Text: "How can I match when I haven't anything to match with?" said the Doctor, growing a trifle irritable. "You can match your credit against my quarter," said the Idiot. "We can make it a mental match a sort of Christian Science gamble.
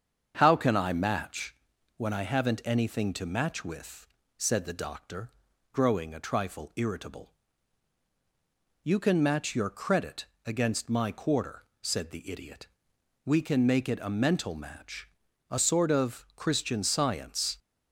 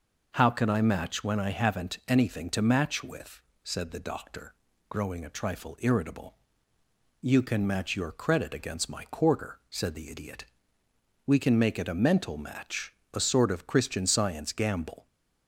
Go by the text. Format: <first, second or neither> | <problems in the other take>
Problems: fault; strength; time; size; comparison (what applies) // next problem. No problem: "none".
second | starts louder than the rest; strong; until 1.3 s; 7.5 dB // pauses between "match" and "when"; at 1.5 s; 0.40 s long // pauses between "credit" and "against"; slight; at 10.2 s; 0.18 s long // pauses between "match" and "a"; at 15.0 s; 0.42 s long; slight in the second // stops before "gamble"; at 17.5 s